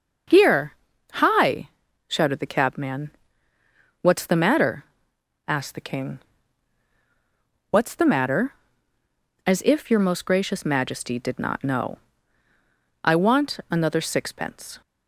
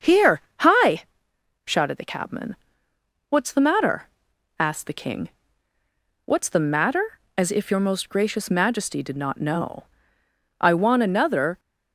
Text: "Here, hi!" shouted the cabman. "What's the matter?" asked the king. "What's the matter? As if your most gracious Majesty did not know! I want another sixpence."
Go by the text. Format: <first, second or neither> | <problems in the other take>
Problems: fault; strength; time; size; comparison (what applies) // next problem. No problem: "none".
first | starts louder than the rest; until 1.7 s; 6.5 dB // stops before "sixpence"; at 11.5 s